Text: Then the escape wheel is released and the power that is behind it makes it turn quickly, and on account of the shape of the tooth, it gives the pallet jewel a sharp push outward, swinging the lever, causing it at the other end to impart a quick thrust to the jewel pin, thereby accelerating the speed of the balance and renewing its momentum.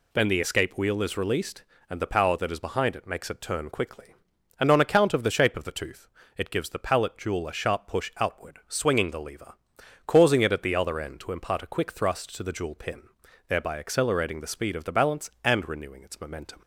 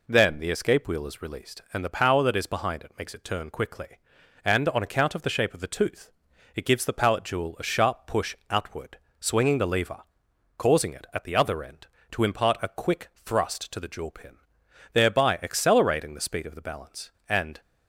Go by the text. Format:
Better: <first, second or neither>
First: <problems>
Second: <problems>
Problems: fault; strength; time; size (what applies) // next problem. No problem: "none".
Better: first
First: none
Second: stops before "renewing its momentum"; at 17.6 s